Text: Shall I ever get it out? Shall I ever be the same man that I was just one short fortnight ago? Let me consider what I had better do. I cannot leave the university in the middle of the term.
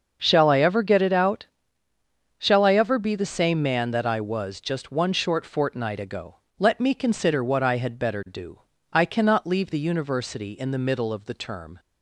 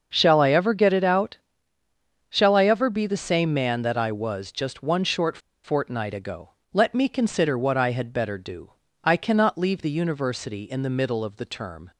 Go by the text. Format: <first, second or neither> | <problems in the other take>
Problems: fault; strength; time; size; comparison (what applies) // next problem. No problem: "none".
first | starts louder than the rest; until 1.1 s; 6.5 dB; also in the first // pauses between "short" and "fortnight"; slight; at 5.3 s; 0.25 s long